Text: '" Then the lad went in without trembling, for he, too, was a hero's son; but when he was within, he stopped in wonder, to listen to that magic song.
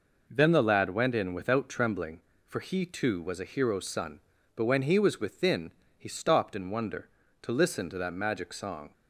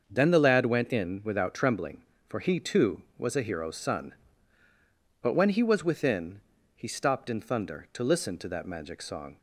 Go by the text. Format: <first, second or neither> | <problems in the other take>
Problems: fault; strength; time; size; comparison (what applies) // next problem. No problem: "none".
first | starts louder than the rest; until 1.0 s; 6.5 dB // says "thunder" for "wonder"; at 7.3 s